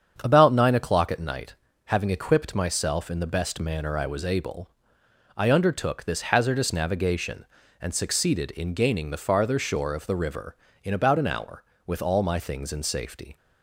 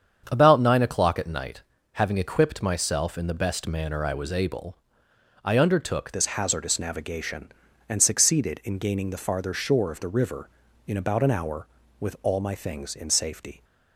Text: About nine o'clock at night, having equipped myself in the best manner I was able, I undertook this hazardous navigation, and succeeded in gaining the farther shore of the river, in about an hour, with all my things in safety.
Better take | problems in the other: first | starts louder than the rest; strong; until 1.3 s; 7.5 dB; strong in the first // changes voice at "this"; from 6.1 s on; 7.5 s long

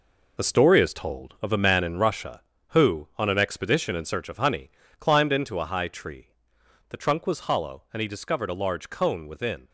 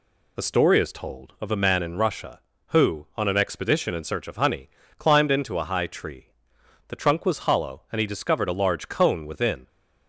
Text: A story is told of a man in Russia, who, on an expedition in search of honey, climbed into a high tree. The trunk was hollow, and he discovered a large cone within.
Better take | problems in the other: second | gets quieter; strong; throughout; 9 dB

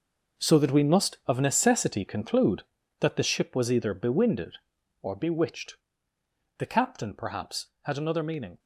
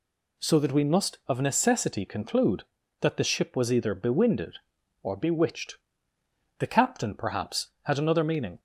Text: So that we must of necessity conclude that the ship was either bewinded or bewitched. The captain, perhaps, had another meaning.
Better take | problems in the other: second | gets quieter; strong; throughout; 11.5 dB

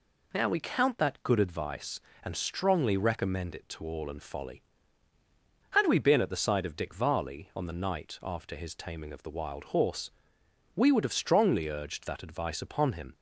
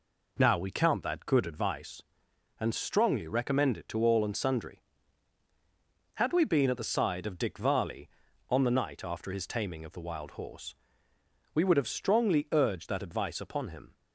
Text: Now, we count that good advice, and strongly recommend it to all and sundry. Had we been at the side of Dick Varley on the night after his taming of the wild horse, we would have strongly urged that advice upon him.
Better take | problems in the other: second | says "folly" for "sundry"; at 4.2 s

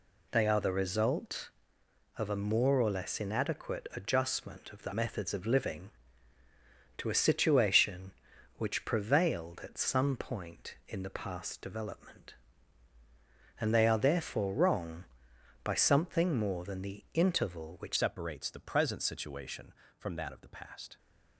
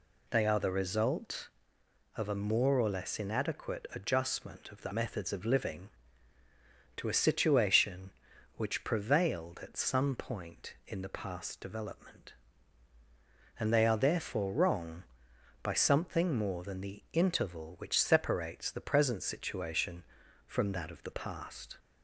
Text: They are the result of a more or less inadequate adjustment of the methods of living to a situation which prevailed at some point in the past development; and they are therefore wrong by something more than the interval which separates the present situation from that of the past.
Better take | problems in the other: second | changes voice at "separates"; from 17.9 s on; 3.0 s long

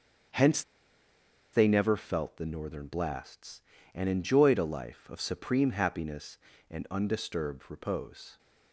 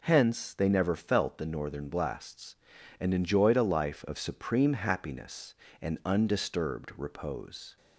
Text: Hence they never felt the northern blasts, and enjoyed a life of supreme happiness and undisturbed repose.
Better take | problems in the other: second | starts louder than the rest; strong; until 2.2 s; 7.5 dB // pauses between "Hence" and "they"; noticeable; at 0.6 s; 0.91 s long

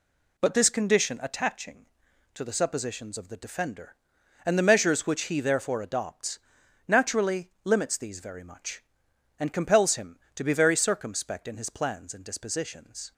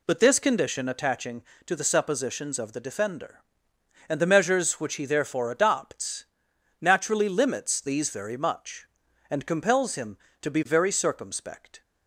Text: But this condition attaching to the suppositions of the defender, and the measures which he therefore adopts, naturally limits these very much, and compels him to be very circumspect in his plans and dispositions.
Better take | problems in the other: first | stops before "in his plans and dispositions"; at 11.8 s

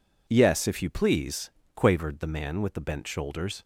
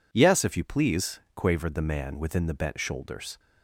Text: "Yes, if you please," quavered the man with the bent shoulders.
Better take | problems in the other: first | says "within" for "with"; at 2.1 s

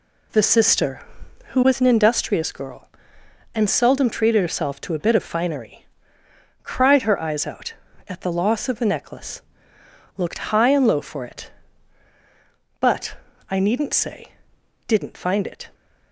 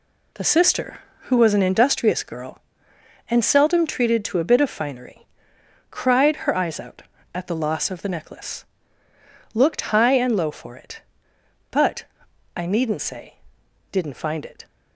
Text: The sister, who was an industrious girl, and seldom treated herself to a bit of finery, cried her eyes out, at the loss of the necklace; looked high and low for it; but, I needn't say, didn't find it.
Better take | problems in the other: first | skips "herself"; at 4.2 s

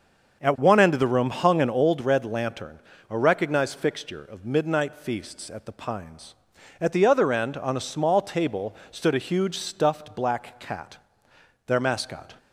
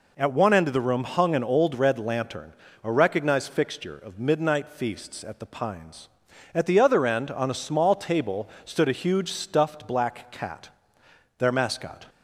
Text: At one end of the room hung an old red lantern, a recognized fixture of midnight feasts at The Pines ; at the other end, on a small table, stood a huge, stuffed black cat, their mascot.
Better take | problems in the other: second | starts louder than the rest; until 1.9 s; 6.5 dB

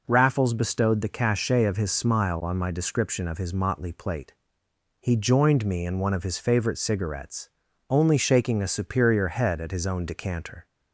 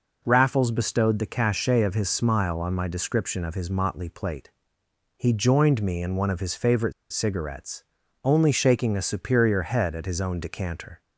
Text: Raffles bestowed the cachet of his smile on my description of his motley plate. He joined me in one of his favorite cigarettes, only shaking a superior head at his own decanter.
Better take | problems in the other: first | pauses between "favorite" and "cigarettes"; slight; at 6.9 s; 0.19 s long

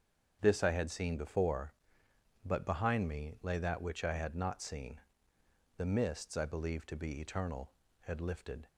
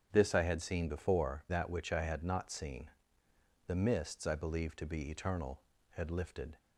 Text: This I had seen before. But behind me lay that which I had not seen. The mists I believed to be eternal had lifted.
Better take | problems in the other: first | starts louder than the rest; strong; until 1.1 s; 8.5 dB; strong in the first // skips "But behind me lay"; at 1.4 s

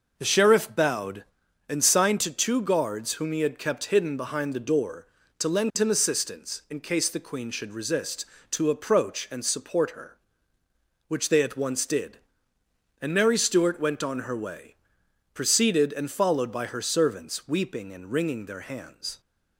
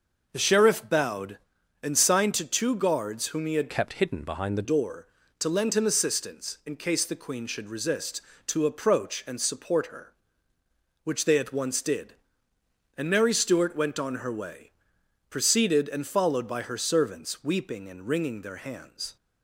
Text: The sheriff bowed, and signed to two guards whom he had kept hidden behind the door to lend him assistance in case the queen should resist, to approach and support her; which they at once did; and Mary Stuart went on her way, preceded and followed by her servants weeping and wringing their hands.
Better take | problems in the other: first | changes voice from "kept" to "the"; from 3.6 to 4.6 s; 1.0 s long

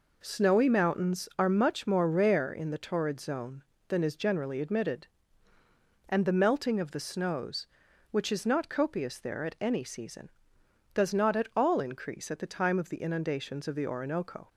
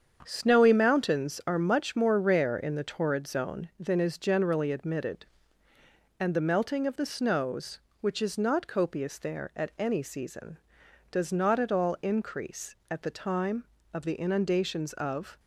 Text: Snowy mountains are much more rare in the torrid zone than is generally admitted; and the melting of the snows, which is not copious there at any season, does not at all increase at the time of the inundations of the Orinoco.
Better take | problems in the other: first | starts louder than the rest; strong; until 1.2 s; 7.5 dB // stops before "the Orinoco"; at 15.3 s

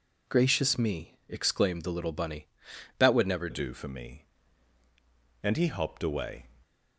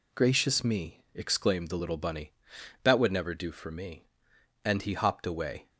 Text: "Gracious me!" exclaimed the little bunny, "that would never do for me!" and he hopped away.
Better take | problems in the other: second | changes voice at "do"; from 3.5 s on; 2.9 s long

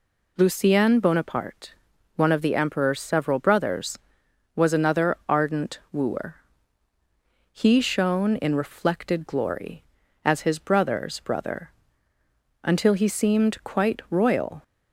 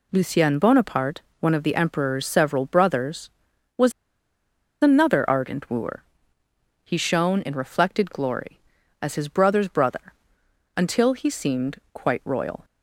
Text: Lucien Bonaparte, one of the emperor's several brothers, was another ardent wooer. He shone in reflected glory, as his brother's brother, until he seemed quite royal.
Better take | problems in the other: first | pauses between "was" and "another"; noticeable; at 3.9 s; 0.90 s long // pauses between "seemed" and "quite"; slight; at 11.7 s; 0.16 s long

